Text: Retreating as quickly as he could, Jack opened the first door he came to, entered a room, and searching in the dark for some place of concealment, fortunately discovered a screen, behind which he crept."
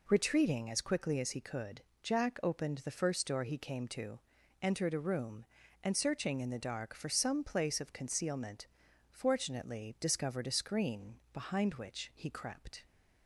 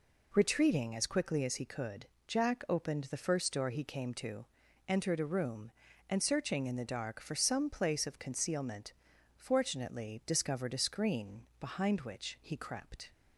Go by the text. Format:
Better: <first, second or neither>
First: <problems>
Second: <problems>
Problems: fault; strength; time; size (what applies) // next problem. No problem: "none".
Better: neither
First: none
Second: none